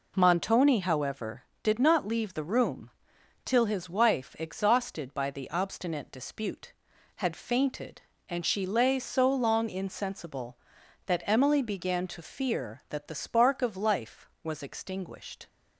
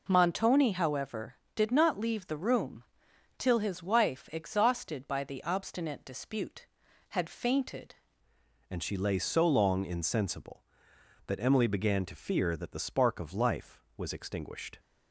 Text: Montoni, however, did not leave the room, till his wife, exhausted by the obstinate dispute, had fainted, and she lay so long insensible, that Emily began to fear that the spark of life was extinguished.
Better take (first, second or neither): first